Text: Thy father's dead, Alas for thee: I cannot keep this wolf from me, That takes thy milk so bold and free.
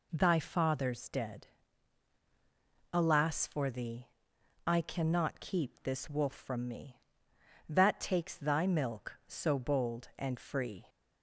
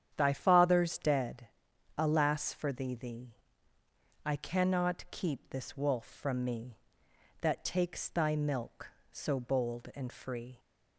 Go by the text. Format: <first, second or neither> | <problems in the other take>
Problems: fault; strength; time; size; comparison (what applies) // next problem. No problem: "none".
first | starts louder than the rest; strong; until 1.1 s; 9 dB // says "thee" twice; at 2.9 s